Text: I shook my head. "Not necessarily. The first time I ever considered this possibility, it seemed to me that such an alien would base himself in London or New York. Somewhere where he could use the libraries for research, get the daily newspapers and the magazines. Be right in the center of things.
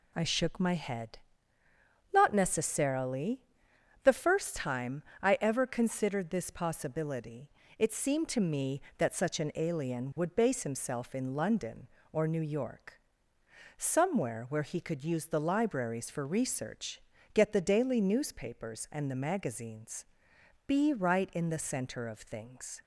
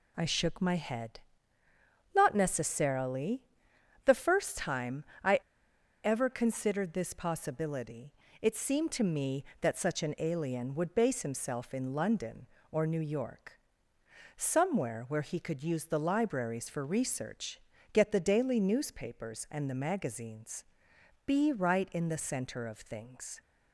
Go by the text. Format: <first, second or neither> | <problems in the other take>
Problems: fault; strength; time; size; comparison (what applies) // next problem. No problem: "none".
first | pauses between "time" and "I"; slight; at 5.0 s; 0.20 s long; slight in the first // pauses between "I" and "ever"; noticeable; at 5.3 s; 0.64 s long